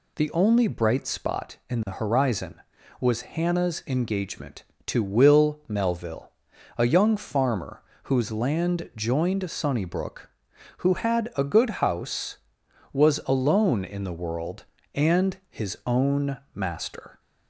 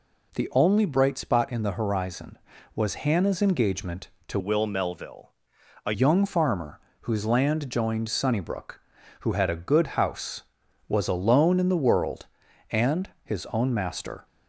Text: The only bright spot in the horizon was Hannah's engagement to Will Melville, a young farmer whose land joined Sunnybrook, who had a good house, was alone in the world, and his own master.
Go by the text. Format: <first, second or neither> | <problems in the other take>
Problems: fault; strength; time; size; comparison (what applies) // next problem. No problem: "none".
first | changes voice from "Will" to "a"; from 4.3 to 5.9 s; 1.6 s long // pauses between "farmer" and "whose"; slight; at 6.7 s; 0.22 s long; slight in the first